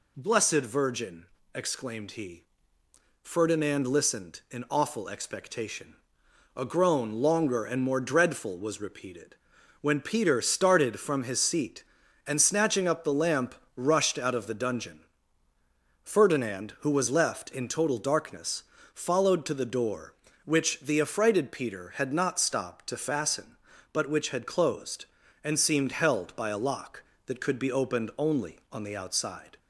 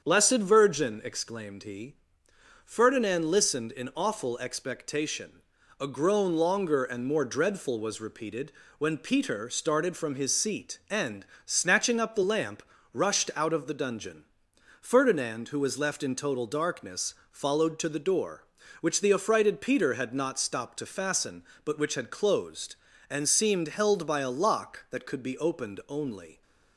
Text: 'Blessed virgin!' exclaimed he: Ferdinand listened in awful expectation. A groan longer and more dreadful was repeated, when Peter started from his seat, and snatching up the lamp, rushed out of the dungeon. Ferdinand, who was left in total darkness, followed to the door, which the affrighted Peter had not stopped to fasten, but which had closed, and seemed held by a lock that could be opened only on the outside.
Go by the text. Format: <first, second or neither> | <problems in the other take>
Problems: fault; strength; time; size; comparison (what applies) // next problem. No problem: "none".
first | starts louder than the rest; strong; until 1.0 s; 7.5 dB // pauses between "and" and "snatching"; slight; at 11.2 s; 0.22 s long // stops before "on the outside"; at 26.4 s